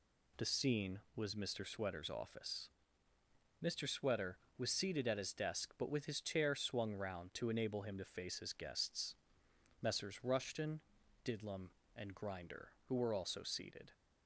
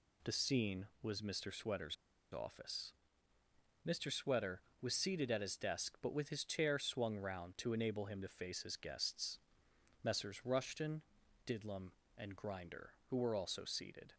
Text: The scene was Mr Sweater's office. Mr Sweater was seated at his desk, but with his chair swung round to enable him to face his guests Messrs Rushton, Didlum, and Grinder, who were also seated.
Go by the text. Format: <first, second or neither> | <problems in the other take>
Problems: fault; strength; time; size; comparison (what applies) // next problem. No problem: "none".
first | pauses between "Sweater's" and "office"; at 1.9 s; 0.37 s long // pauses between "guests" and "Messrs"; noticeable; at 9.3 s; 0.66 s long; noticeable in the first